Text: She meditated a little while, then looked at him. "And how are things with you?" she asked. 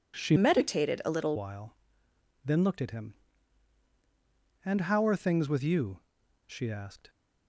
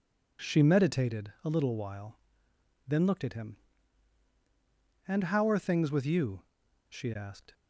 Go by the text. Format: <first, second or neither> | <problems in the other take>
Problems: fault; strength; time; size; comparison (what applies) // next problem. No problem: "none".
second | changes voice from "meditated" to "little"; from 0.3 to 1.3 s; 1.0 s long